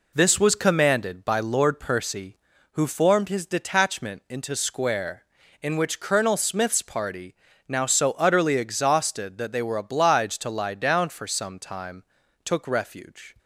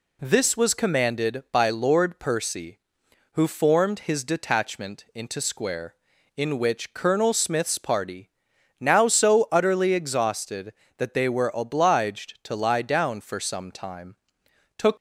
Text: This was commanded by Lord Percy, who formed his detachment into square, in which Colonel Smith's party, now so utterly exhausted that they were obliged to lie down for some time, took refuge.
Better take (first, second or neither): first